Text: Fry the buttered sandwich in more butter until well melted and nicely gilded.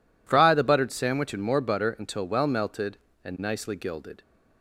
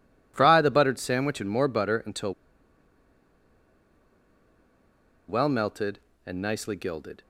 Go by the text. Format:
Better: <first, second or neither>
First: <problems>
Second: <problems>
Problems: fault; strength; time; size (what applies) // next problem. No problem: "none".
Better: first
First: none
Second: pauses between "until" and "well"; strong; at 2.3 s; 2.9 s long